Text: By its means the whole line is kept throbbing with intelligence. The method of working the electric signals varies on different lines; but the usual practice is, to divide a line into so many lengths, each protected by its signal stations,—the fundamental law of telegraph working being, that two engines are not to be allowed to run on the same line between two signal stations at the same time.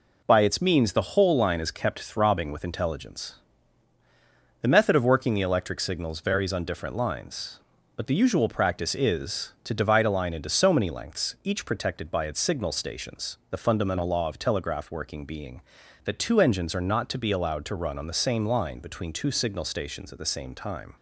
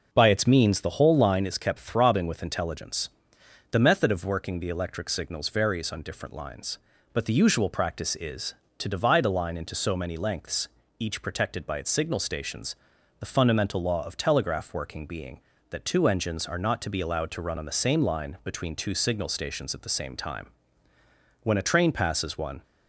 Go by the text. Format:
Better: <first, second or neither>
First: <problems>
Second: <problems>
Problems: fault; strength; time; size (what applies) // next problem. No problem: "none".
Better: first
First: none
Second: goes on to say "When a train passes one"; noticeable; from 21.4 s on; 1.1 s long